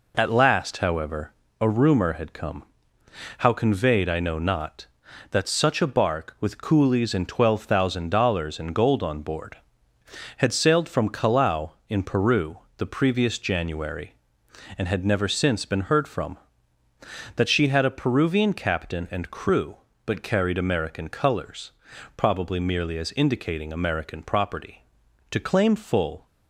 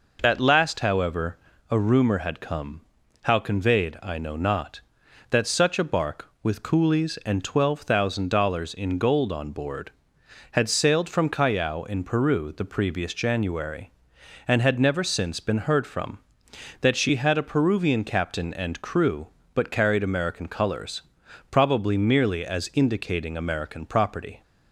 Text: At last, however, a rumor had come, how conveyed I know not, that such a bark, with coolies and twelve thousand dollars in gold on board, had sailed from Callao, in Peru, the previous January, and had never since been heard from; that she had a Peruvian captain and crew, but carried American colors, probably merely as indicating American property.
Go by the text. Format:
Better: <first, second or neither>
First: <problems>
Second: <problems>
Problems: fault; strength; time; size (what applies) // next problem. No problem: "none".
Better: second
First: goes on to say "To claim full"; noticeable; from 25.3 s on; 0.94 s long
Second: none